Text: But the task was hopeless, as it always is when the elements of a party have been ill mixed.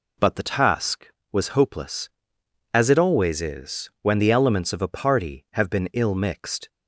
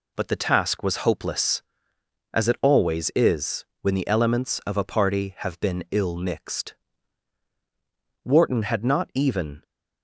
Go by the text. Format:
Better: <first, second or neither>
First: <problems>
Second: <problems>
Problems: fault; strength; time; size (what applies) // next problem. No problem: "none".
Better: first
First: none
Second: pauses between "is" and "when"; slight; at 3.6 s; 0.16 s long // goes on to say "Wharton had not even"; from 8.2 s on; 1.4 s long